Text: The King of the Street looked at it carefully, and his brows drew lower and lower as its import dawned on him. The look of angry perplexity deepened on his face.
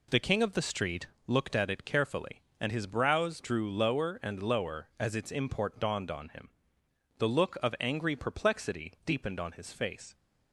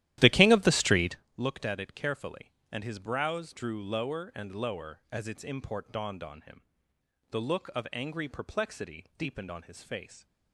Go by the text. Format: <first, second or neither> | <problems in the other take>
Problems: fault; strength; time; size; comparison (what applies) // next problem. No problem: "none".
first | starts louder than the rest; strong; until 1.2 s; 14 dB // pauses between "Street" and "looked"; slight; at 1.1 s; 0.22 s long; slight in the first